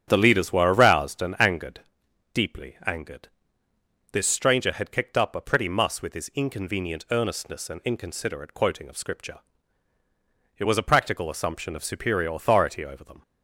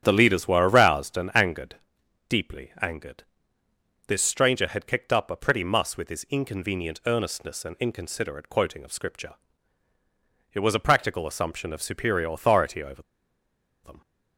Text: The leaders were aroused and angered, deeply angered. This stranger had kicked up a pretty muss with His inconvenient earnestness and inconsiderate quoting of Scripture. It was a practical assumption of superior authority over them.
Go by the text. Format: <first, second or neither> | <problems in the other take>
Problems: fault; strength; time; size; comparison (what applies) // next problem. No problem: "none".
first | starts louder than the rest; strong; until 1.0 s; 9.5 dB; strong in the first // pauses between "over" and "them"; noticeable; at 13.0 s; 0.83 s long